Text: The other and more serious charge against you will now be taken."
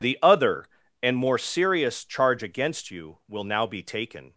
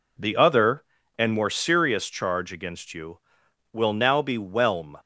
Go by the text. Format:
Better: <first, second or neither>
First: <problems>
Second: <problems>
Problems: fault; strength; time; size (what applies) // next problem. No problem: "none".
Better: first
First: none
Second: says "whelm" for "taken"; at 4.3 s